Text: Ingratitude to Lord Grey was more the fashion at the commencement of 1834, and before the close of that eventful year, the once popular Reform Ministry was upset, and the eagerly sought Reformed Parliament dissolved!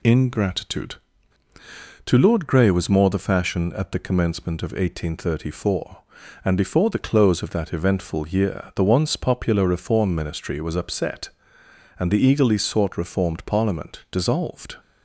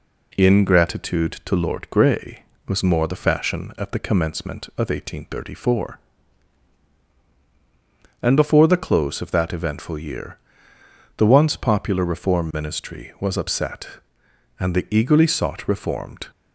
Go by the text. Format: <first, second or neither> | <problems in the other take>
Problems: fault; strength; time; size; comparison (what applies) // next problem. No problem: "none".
first | stops before "Parliament dissolved"; at 16.3 s